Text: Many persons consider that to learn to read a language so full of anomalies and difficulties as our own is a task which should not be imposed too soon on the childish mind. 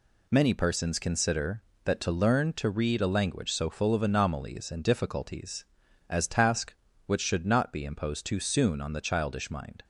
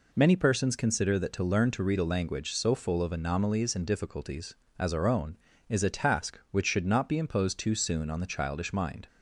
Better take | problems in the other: second | skips "our own is a"; at 6.2 s

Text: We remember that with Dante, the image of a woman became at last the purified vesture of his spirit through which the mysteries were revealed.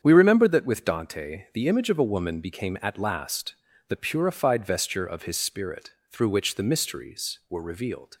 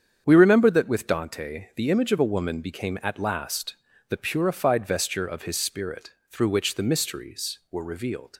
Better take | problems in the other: neither | starts louder than the rest; strong; the same in both // pauses between "last" and "the"; slight; the same in both // pauses between "spirit" and "through"; slight; the same in both

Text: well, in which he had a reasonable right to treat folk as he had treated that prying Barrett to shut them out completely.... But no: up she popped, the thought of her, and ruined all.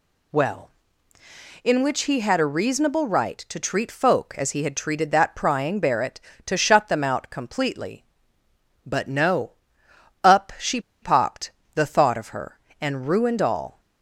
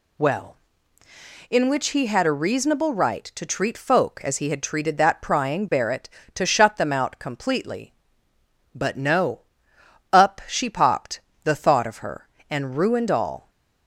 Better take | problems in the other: second | pauses between "she" and "popped"; slight; at 10.8 s; 0.21 s long

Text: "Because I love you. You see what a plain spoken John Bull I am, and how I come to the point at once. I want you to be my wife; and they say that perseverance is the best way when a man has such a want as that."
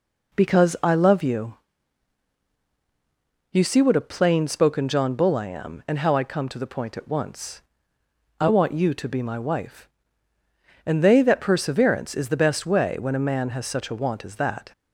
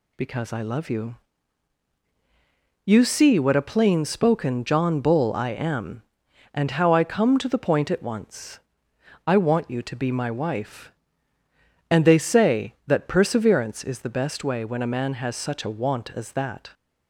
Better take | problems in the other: second | skips "say"; at 11.1 s

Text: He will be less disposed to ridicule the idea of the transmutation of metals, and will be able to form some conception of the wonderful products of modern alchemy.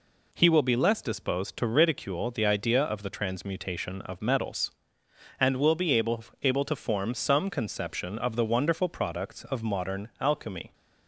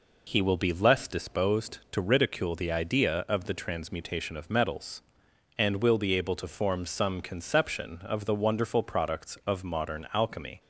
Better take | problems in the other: second | says "able" twice; at 6.4 s

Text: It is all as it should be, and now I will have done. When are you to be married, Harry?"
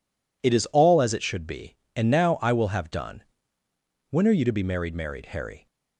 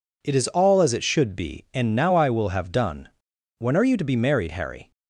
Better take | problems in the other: second | says "married" twice; at 4.9 s

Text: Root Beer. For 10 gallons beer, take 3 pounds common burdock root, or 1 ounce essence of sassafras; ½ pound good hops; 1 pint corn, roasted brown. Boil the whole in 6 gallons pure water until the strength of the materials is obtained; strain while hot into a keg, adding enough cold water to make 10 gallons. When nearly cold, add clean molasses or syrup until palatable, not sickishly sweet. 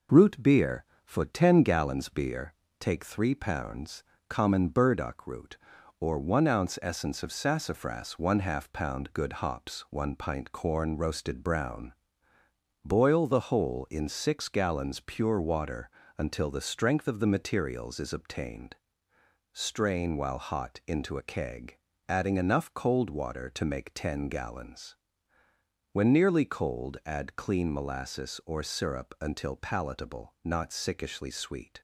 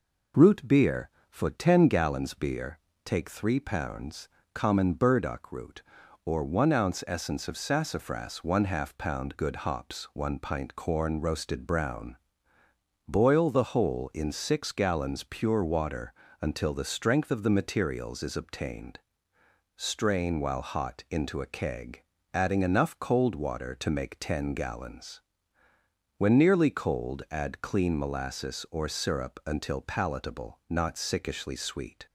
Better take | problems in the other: second | gets quieter; throughout; 3.5 dB // pauses between "pounds" and "common"; slight; at 4.0 s; 0.26 s long; slight in the second // pauses between "water" and "until"; slight; at 15.8 s; 0.30 s long; slight in the second

